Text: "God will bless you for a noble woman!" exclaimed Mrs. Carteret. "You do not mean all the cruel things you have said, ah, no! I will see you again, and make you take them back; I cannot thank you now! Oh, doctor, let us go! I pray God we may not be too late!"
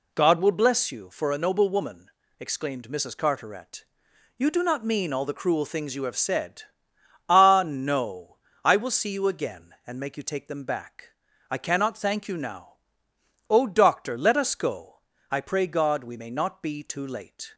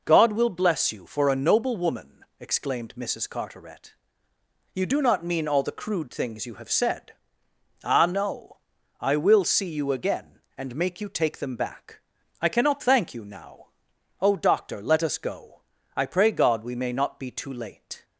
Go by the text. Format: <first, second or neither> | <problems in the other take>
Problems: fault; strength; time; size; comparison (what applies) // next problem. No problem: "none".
first | says "crude" for "cruel"; at 5.7 s